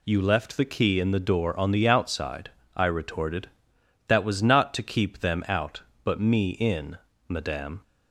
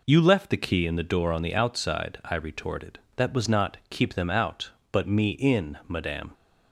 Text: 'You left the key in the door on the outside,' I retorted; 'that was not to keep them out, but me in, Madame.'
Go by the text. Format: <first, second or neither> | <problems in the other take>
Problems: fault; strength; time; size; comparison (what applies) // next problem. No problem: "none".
first | skips "to"; at 3.8 s